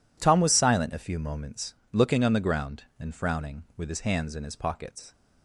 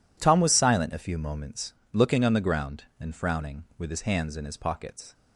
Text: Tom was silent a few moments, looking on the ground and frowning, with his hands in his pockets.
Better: neither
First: none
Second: none

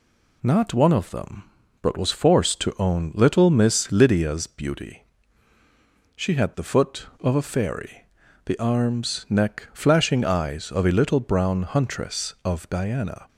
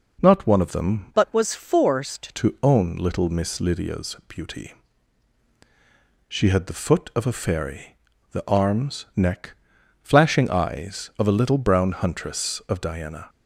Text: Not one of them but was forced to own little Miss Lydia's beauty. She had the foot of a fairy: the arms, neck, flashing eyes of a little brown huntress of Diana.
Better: first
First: none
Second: changes voice from "but" to "forced"; from 1.1 to 2.3 s; 1.2 s long

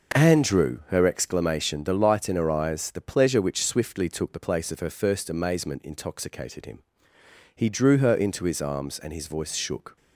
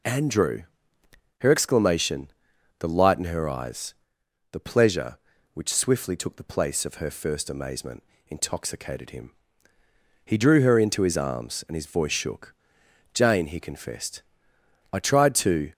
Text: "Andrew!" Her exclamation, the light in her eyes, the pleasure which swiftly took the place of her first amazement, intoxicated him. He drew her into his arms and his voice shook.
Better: first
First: none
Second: goes on to say "Jane he confessed I tried to"; strong; from 13.1 s on; 2.5 s long

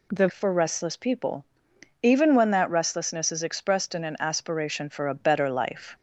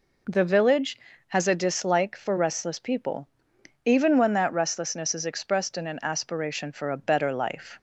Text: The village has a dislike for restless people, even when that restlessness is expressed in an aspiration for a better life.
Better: second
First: skips "village has a dislike"; at 0.2 s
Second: none

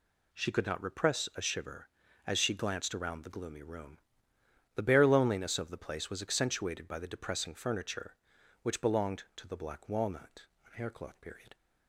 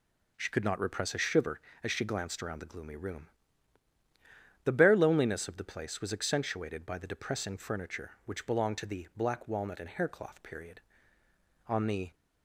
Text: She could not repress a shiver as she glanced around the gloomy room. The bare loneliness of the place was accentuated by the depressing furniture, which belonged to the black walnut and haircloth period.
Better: first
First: none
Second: goes on to say "On the"; slight; from 11.6 s on; 0.48 s long

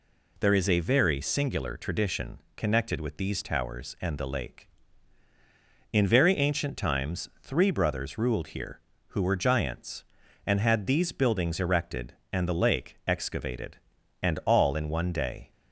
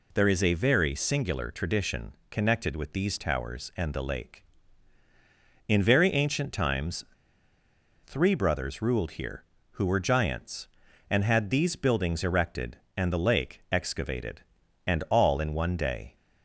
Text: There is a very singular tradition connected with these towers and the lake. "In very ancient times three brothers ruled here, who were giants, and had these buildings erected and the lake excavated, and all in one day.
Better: first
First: pauses between "tradition" and "connected"; slight; at 2.3 s; 0.18 s long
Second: pauses between "tradition" and "connected"; slight; at 2.1 s; 0.18 s long // pauses between "times" and "three"; at 7.0 s; 1.0 s long

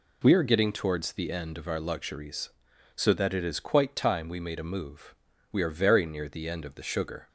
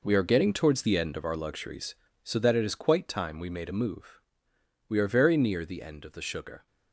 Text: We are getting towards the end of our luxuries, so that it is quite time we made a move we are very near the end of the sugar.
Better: first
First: pauses between "move" and "we"; slight; at 5.1 s; 0.34 s long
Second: gets quieter; strong; throughout; 10.5 dB // pauses between "move" and "we"; noticeable; at 4.1 s; 0.70 s long

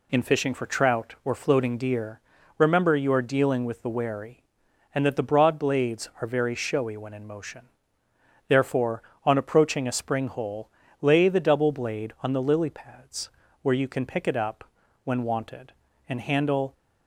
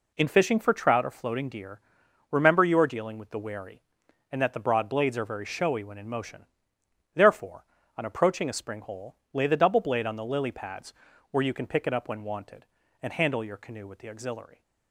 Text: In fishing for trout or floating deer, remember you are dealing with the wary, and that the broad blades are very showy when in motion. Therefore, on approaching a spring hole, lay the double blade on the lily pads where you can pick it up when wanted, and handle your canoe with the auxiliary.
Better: second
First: pauses between "pads" and "where"; slight; at 13.2 s; 0.32 s long // pauses between "up" and "when"; at 14.6 s; 0.40 s long // stops before "your canoe with the auxiliary"; at 16.7 s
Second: pauses between "pads" and "where"; at 10.9 s; 0.38 s long

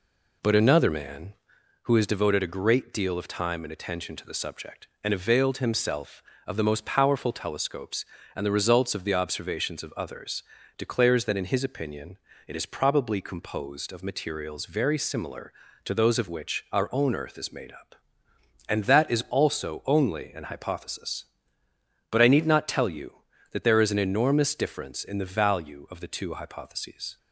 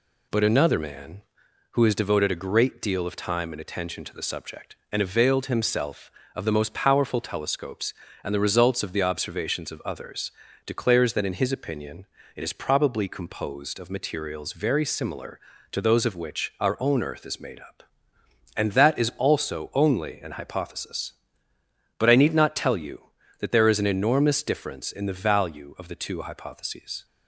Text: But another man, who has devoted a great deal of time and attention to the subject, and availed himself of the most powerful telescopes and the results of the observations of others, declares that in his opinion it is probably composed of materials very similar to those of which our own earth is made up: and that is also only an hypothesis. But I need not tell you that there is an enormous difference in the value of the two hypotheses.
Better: second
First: starts louder than the rest; slight; until 1.8 s; 3 dB // pauses between "opinion" and "it"; slight; at 12.1 s; 0.32 s long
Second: pauses between "opinion" and "it"; slight; at 12.0 s; 0.32 s long

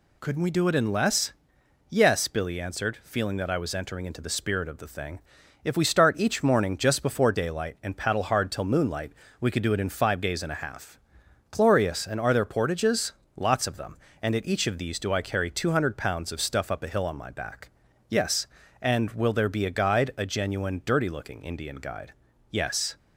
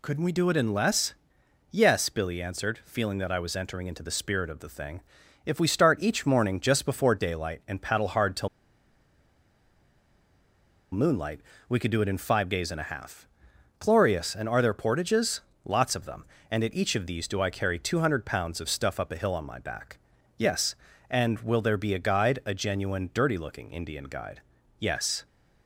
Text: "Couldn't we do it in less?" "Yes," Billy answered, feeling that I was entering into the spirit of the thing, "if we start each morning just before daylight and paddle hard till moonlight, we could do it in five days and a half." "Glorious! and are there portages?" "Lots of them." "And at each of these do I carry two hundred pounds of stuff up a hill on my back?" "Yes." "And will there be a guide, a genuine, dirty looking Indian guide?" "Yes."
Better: first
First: none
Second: pauses between "till" and "moonlight"; strong; at 8.4 s; 2.4 s long

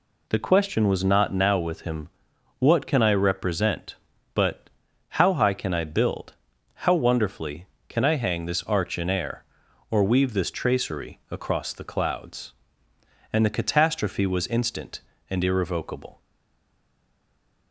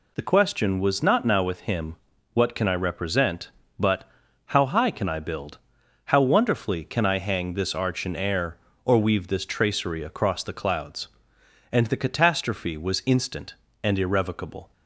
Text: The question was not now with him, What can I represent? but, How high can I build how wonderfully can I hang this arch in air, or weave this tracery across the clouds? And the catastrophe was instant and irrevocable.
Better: second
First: pauses between "build" and "how"; noticeable; at 6.3 s; 0.48 s long // stays silent after the last word; noticeable; from 16.2 s on; 1.5 s long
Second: pauses between "build" and "how"; noticeable; at 5.5 s; 0.48 s long

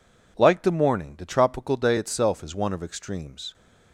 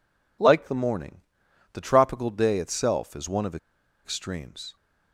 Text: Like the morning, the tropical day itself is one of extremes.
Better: first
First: none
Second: pauses between "of" and "extremes"; noticeable; at 3.5 s; 0.48 s long

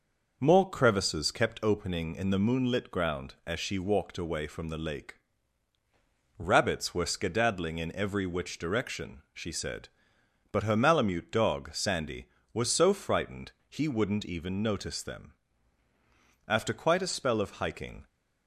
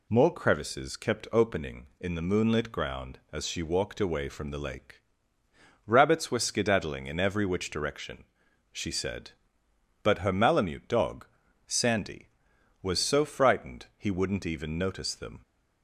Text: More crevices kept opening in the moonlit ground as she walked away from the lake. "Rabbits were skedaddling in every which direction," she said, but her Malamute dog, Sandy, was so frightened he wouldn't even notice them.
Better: second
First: pauses between "frightened" and "he"; slight; at 13.5 s; 0.16 s long // goes on to say "After quite a spell of hiking"; from 16.4 s on; 1.5 s long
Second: none

